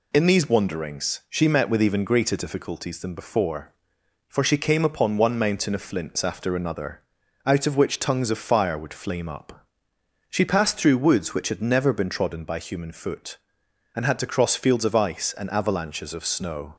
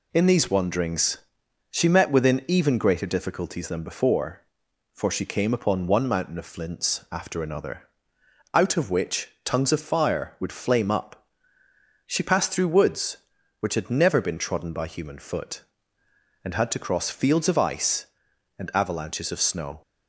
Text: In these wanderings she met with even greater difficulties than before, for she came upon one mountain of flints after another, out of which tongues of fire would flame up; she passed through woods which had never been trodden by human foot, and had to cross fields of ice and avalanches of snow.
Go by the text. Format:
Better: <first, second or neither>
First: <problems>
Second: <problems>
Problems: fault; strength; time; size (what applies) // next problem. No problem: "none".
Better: first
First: none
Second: pauses between "wanderings" and "she"; noticeable; at 1.1 s; 0.52 s long // says "within" for "with"; at 2.0 s